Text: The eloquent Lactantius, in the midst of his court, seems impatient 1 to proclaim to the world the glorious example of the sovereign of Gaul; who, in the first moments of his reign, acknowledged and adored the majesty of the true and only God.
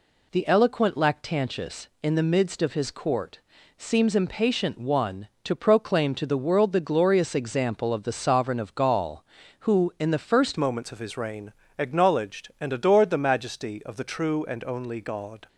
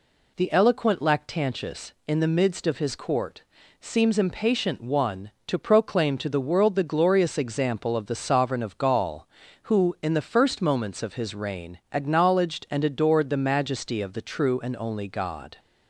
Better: second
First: changes voice at "moments"; from 10.5 s on; 4.9 s long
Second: none

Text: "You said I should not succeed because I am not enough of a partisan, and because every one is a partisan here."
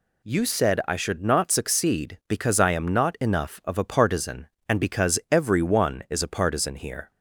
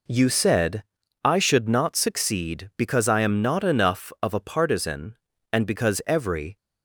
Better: first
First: none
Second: pauses between "said" and "I"; at 0.8 s; 0.40 s long // stops before "one is a partisan here"; at 6.5 s

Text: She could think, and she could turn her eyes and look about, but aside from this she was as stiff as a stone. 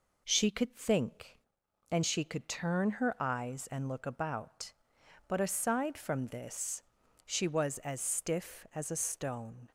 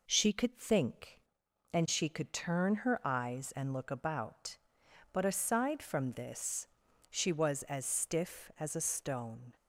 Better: neither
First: pauses between "this" and "she"; at 6.8 s; 0.44 s long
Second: pauses between "this" and "she"; at 6.6 s; 0.44 s long

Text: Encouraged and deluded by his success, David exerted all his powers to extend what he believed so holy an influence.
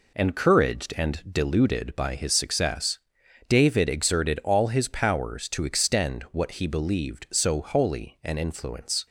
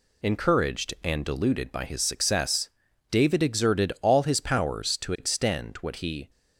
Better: first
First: none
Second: stops before "believed so holy an influence"; at 6.2 s

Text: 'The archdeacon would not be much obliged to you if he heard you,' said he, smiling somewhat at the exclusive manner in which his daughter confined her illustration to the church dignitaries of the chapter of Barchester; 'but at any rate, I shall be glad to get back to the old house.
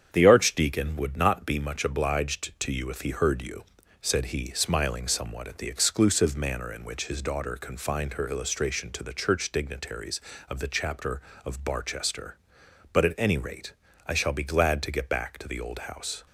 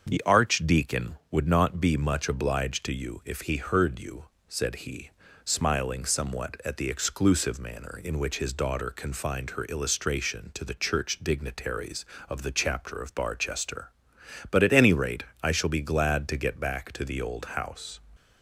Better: neither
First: starts louder than the rest; strong; until 1.1 s; 8 dB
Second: starts louder than the rest; until 1.1 s; 6.5 dB

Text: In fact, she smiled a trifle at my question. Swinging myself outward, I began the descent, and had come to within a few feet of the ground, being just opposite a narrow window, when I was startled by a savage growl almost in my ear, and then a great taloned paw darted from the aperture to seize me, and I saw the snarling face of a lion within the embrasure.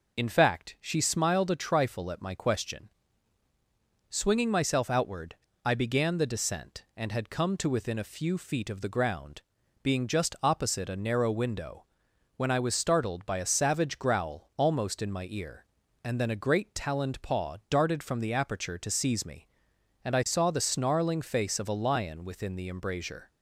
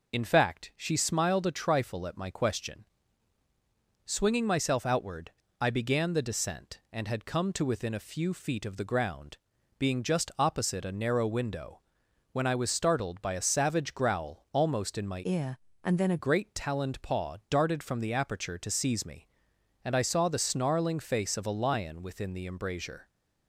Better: first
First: none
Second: changes voice from "ear" to "a"; from 15.2 to 16.1 s; 0.9 s long

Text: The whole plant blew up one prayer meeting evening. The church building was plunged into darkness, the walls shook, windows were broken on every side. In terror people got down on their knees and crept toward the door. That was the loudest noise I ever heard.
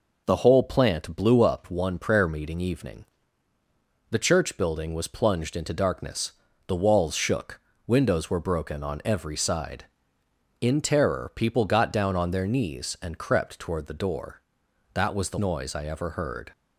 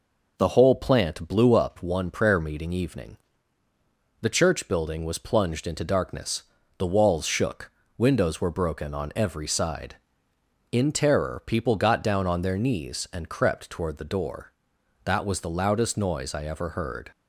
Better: second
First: skips "loudest"; at 15.3 s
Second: none

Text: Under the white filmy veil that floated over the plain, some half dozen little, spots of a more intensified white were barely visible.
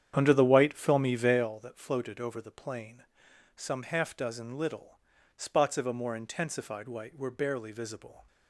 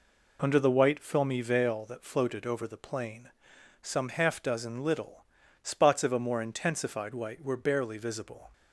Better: second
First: starts louder than the rest; strong; until 1.5 s; 9 dB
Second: none

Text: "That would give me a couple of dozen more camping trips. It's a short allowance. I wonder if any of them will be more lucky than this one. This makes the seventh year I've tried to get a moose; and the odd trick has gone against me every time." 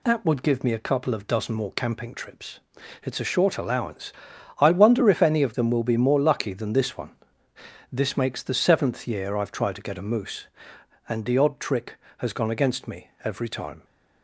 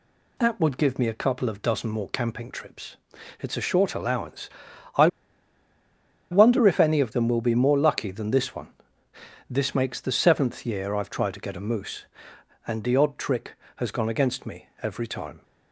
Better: first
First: pauses between "me" and "every"; slight; at 13.0 s; 0.16 s long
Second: pauses between "I" and "wonder"; at 5.0 s; 1.2 s long // pauses between "me" and "every"; slight; at 14.6 s; 0.16 s long

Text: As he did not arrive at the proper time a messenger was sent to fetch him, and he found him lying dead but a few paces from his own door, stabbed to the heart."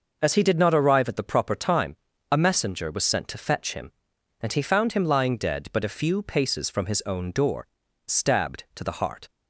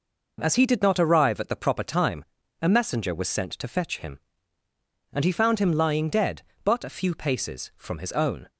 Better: first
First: pauses between "time" and "a"; slight; at 1.9 s; 0.36 s long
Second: pauses between "time" and "a"; at 2.2 s; 0.38 s long // stops before "door stabbed to the heart"; at 8.4 s

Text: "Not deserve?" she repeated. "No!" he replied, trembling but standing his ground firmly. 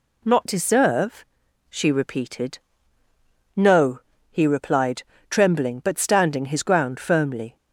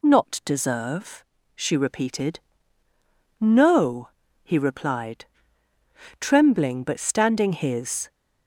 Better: first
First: none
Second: stops before "ground firmly"; at 8.0 s

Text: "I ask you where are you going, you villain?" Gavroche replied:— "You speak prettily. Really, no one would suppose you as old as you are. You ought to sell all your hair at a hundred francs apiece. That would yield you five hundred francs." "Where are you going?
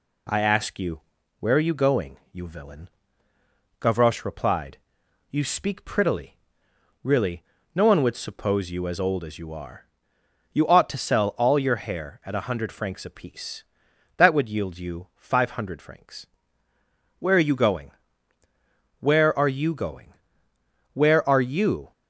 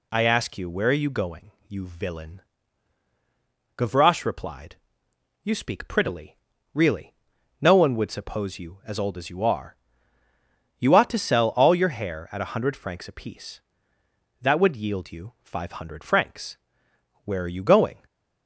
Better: second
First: pauses between "you" and "where"; at 0.9 s; 0.40 s long // goes on to say "Where are you going Where are you"; strong; from 18.9 s on; 2.9 s long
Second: none

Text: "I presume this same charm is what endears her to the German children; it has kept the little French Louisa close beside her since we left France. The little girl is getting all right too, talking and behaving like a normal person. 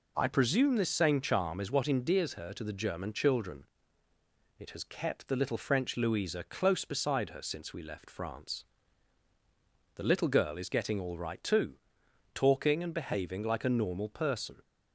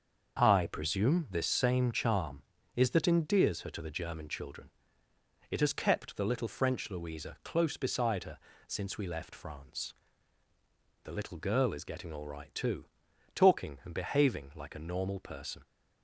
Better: first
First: none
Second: starts louder than the rest; until 1.4 s; 6.5 dB // says "that" for "what"; at 2.9 s // pauses between "her" and "since"; slight; at 8.3 s; 0.30 s long

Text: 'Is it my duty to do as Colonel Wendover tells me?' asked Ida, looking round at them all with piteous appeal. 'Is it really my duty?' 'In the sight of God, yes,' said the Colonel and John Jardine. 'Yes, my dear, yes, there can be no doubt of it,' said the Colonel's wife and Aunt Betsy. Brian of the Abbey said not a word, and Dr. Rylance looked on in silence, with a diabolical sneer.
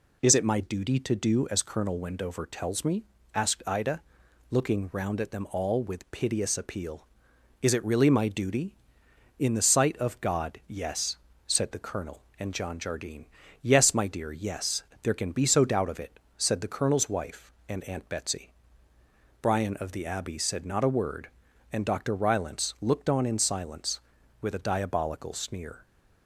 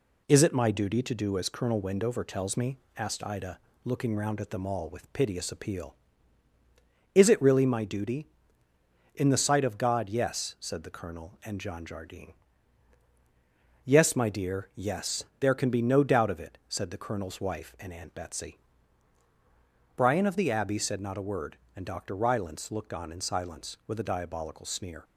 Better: second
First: says "so" for "no"; at 15.4 s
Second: none

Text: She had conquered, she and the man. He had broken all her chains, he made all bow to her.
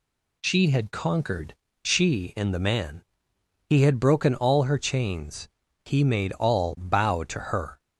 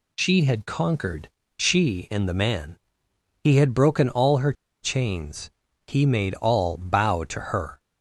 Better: first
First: none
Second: pauses between "her" and "chains"; slight; at 4.5 s; 0.30 s long

